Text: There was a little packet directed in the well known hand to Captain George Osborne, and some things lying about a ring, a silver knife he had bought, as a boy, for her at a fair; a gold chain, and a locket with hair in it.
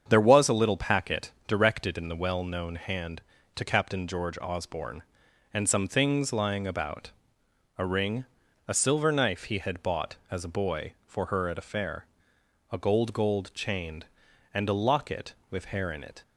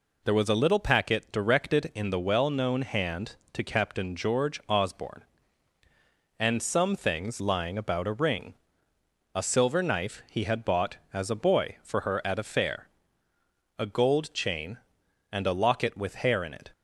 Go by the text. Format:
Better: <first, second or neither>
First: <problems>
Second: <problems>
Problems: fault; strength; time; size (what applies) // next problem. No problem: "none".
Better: second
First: starts louder than the rest; strong; until 1.1 s; 7.5 dB // pauses between "packet" and "directed"; slight; at 1.3 s; 0.16 s long // pauses between "about" and "a"; noticeable; at 7.1 s; 0.68 s long // says "gold" twice; at 13.1 s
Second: none